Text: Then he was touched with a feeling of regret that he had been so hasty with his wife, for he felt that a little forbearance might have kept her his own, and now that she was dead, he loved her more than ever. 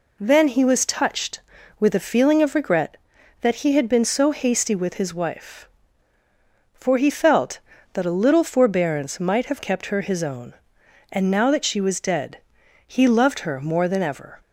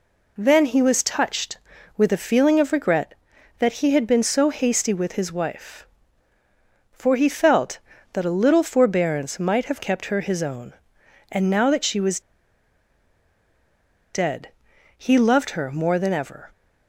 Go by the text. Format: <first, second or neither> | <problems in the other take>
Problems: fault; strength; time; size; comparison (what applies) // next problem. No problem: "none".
first | pauses between "was" and "dead"; strong; at 12.1 s; 1.9 s long